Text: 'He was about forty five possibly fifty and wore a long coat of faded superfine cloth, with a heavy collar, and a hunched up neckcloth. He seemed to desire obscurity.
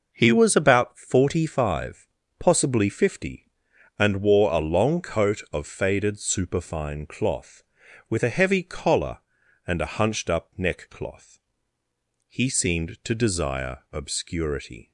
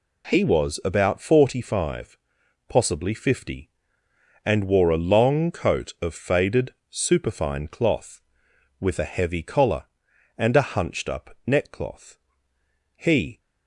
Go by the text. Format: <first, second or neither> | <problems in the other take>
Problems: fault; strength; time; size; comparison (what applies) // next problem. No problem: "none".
first | pauses between "five" and "possibly"; noticeable; at 2.1 s; 0.50 s long; slight in the first // pauses between "faded" and "superfine"; slight; at 6.7 s; 0.16 s long // stops before "seemed to desire obscurity"; at 13.3 s